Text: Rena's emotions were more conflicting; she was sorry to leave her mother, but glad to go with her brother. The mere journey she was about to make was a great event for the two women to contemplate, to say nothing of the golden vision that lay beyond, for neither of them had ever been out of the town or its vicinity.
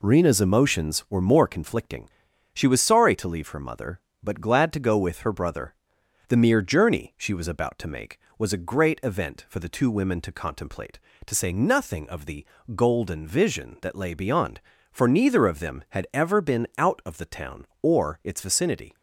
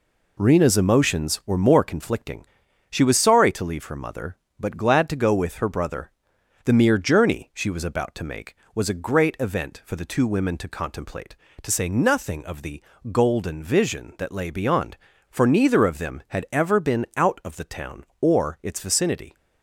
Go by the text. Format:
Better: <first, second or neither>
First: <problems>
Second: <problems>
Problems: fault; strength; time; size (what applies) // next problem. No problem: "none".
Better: neither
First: pauses between "the" and "golden"; slight; at 12.4 s; 0.30 s long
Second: pauses between "the" and "golden"; slight; at 12.8 s; 0.30 s long